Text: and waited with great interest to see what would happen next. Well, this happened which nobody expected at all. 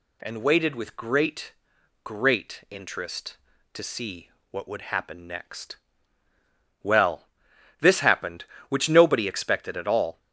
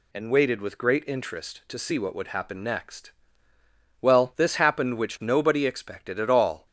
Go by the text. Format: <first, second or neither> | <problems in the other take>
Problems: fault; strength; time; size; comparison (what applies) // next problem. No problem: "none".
second | says "great" twice; at 2.0 s // pauses between "see" and "what"; slight; at 4.2 s; 0.22 s long